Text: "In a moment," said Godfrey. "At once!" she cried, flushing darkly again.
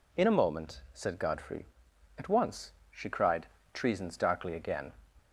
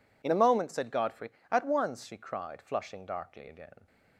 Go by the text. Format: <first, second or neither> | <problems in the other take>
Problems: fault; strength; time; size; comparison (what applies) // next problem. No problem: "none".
second | says "treasons" for "flushing"; at 3.7 s